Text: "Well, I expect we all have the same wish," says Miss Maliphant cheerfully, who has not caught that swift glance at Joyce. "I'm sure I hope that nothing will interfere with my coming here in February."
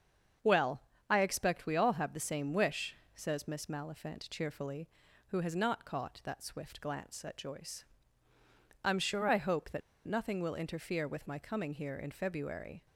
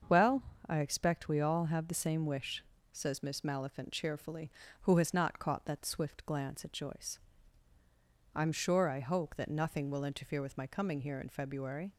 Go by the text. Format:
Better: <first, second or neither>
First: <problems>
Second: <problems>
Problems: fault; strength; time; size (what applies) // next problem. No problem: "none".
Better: second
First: starts louder than the rest; until 1.7 s; 7 dB // pauses between "that" and "nothing"; slight; at 9.8 s; 0.26 s long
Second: starts louder than the rest; until 1.3 s; 6.5 dB